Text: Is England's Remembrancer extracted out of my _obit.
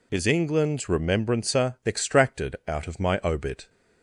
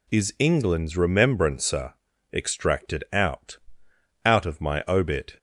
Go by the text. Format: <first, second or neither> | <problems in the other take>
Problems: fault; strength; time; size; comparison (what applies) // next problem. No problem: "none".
first | pauses between "Remembrancer" and "extracted"; at 1.9 s; 0.40 s long // says "out" twice; at 4.2 s